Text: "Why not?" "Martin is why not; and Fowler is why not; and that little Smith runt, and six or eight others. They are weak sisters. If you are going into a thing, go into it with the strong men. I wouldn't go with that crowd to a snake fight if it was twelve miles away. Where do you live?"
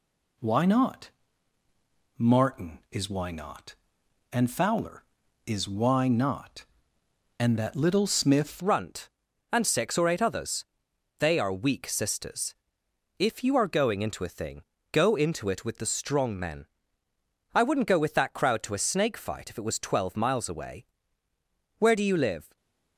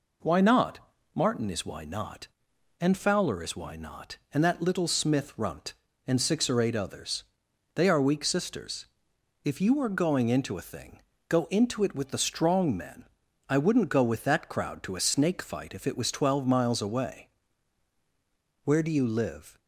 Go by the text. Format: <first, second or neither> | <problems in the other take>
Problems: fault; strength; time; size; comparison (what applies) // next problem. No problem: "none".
second | changes voice at "runt"; from 8.5 s on; 14.0 s long // stays silent after the last word; slight; from 22.4 s on; 0.5 s long